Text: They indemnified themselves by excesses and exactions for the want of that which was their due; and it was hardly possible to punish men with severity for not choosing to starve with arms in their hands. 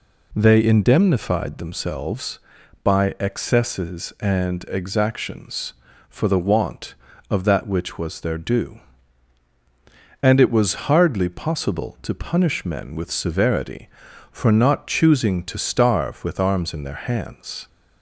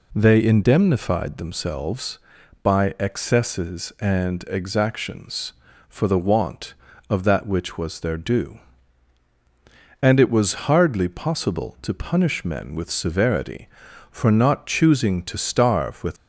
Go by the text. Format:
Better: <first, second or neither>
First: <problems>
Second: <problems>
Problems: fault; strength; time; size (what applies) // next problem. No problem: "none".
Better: first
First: none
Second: stops before "arms in their hands"; at 16.1 s